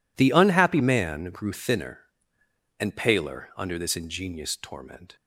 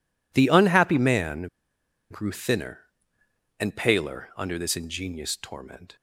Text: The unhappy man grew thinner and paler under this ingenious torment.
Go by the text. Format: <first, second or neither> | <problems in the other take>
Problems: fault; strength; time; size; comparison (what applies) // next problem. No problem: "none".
first | pauses between "man" and "grew"; noticeable; at 1.4 s; 0.62 s long